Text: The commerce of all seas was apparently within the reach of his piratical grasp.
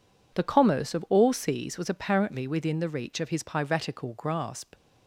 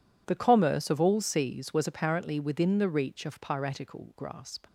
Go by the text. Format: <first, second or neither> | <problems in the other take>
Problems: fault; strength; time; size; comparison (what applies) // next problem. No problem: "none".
first | skips "his"; at 3.4 s